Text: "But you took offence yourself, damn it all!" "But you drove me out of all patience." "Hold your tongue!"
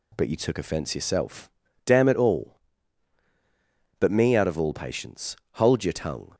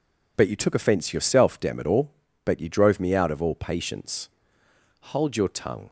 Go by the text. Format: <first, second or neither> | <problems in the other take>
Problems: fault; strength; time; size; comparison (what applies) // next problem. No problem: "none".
second | skips "you drove"; at 4.1 s